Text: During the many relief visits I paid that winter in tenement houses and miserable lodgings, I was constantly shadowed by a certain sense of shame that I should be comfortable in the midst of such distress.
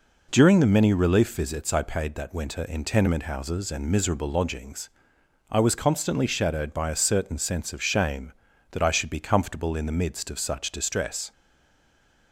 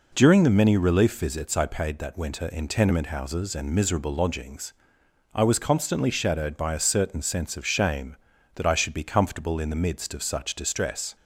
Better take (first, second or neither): second